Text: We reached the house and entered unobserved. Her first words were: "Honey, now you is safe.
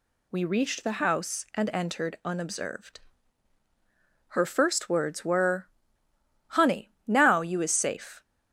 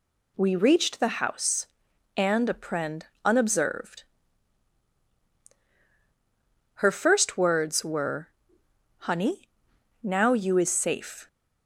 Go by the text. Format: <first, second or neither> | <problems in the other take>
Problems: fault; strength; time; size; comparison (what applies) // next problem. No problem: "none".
first | says "apprend" for "entered"; at 2.4 s